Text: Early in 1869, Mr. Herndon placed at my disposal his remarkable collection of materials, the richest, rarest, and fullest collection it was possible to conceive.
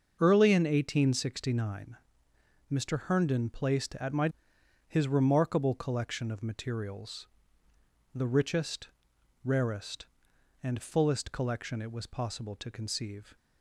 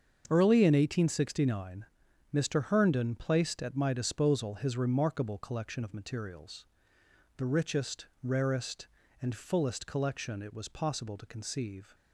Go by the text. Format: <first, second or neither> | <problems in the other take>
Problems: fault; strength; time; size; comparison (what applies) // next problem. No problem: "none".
second | starts louder than the rest; until 1.2 s; 6.5 dB; also in the second // skips "disposal"; at 4.5 s